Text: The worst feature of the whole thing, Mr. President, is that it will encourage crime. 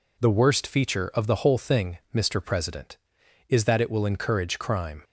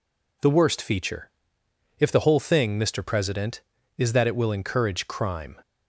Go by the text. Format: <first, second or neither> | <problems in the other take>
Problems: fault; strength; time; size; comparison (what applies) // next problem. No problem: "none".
first | says "if" for "of"; at 1.9 s